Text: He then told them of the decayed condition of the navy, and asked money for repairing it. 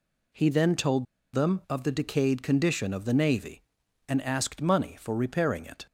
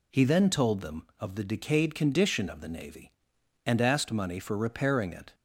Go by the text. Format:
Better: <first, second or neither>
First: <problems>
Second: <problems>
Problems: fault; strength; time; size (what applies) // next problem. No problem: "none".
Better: second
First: pauses between "told" and "them"; slight; at 1.0 s; 0.28 s long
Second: none